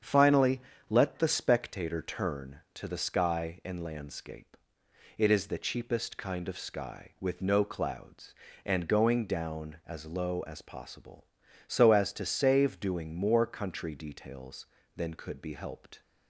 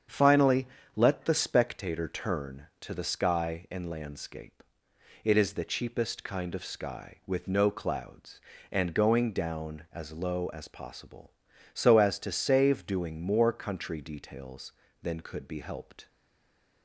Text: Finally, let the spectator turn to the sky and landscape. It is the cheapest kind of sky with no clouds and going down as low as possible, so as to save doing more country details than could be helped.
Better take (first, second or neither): first